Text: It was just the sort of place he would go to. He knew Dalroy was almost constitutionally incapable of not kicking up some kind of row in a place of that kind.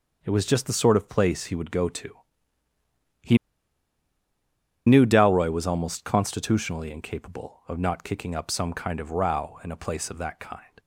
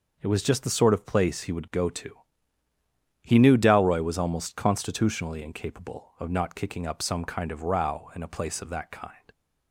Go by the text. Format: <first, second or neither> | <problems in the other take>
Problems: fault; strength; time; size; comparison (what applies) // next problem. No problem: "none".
second | pauses between "He" and "knew"; strong; at 3.3 s; 1.4 s long